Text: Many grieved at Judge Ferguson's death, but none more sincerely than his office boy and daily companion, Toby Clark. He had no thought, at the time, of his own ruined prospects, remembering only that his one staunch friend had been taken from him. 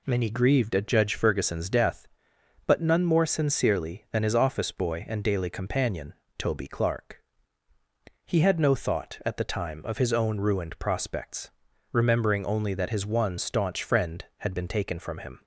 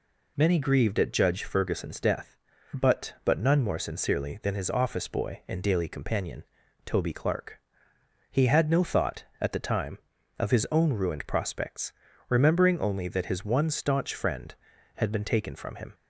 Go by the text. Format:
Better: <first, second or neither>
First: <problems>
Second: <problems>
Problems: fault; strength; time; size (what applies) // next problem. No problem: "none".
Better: first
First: none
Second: says "but" twice; at 3.2 s